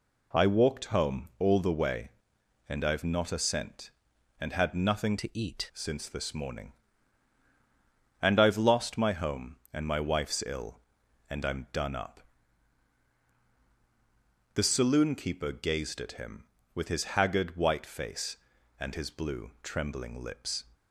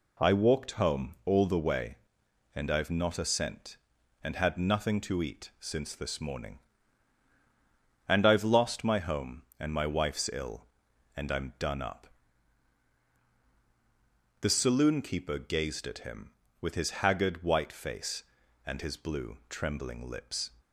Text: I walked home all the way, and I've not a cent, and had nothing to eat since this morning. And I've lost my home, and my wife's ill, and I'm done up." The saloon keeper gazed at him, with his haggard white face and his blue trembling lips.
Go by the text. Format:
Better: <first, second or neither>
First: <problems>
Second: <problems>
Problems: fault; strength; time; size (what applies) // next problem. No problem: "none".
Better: second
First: changes voice from "to" to "eat"; from 5.1 to 5.7 s; 0.6 s long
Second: none